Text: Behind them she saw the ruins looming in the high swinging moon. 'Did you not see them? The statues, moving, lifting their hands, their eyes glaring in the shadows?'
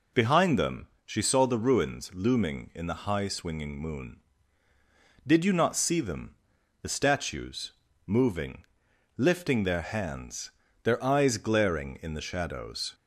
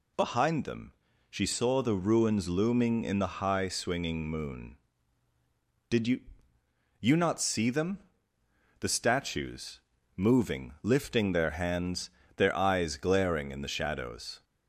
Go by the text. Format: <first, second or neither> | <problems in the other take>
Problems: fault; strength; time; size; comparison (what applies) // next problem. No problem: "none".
first | pauses between "them" and "she"; at 0.9 s; 0.38 s long; slight in the first // says "you" twice; at 6.9 s